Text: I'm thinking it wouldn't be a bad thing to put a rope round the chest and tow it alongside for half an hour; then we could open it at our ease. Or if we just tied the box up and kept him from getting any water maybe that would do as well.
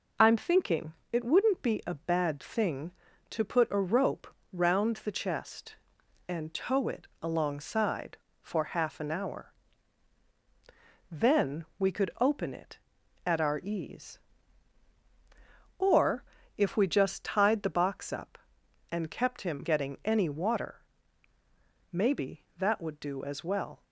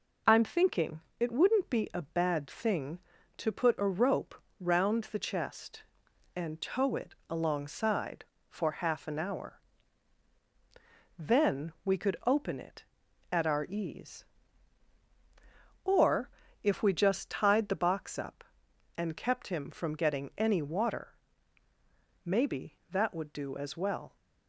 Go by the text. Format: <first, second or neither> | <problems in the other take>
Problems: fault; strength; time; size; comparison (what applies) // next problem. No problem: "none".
second | pauses between "thinking" and "it"; slight; at 0.9 s; 0.20 s long; slight in the second // pauses between "rope" and "round"; slight; at 4.2 s; 0.24 s long; slight in the second // pauses between "then" and "we"; slight; at 11.6 s; 0.16 s long // pauses between "Or" and "if"; slight; at 16.2 s; 0.34 s long; slight in the second // skips "from"; at 19.6 s // pauses between "water" and "maybe"; at 20.8 s; 1.1 s long; also in the second